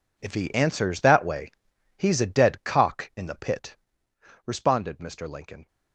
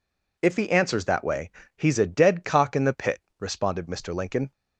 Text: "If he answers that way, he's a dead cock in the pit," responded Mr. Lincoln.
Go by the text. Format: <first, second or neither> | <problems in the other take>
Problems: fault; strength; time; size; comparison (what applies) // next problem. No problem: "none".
second | gets quieter; strong; throughout; 14 dB